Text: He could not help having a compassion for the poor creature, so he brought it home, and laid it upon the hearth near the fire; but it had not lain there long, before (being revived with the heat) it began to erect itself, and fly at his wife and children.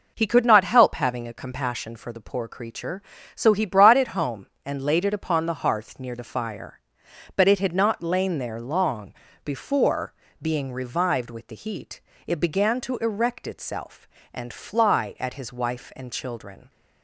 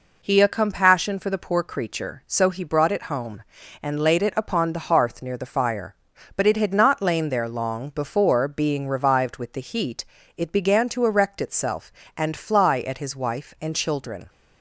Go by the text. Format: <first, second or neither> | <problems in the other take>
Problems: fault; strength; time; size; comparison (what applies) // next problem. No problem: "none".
first | skips "could not help having"; at 0.3 s